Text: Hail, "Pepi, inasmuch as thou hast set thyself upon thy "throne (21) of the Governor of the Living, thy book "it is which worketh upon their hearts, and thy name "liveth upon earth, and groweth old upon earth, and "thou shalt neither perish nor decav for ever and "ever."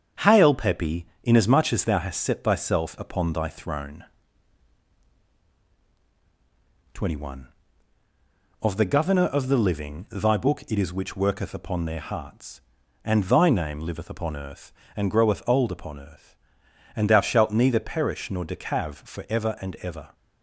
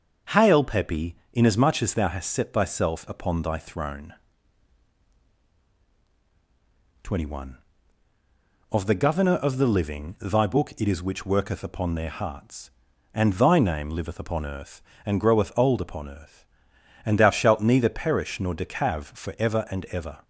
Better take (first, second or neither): second